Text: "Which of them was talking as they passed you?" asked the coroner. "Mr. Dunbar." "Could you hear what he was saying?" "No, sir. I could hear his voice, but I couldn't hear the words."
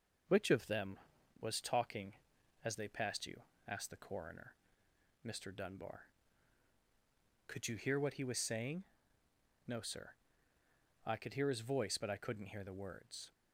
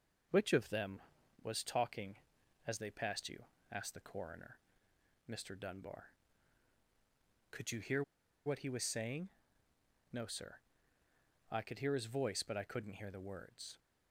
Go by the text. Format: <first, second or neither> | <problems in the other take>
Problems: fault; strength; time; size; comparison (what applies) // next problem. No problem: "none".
first | pauses between "hear" and "what"; at 8.0 s; 0.42 s long